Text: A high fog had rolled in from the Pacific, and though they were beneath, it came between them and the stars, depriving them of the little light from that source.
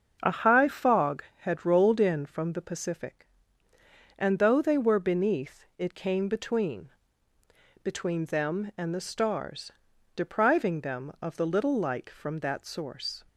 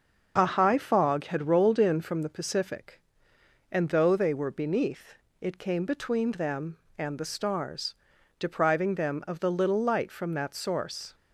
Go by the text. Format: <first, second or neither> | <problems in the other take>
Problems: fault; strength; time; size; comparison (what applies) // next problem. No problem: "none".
second | starts louder than the rest; until 1.4 s; 6.5 dB; also in the second // says "between" twice; at 7.8 s